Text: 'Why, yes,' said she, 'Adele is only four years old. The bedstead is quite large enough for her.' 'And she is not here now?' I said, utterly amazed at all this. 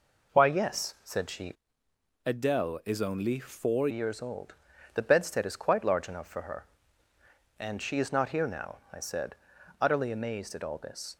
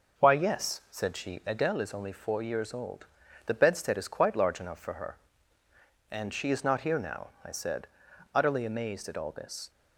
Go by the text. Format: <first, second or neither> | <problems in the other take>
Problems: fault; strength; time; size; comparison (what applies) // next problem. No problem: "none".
second | changes voice from "Adele" to "four"; from 2.2 to 3.8 s; 1.6 s long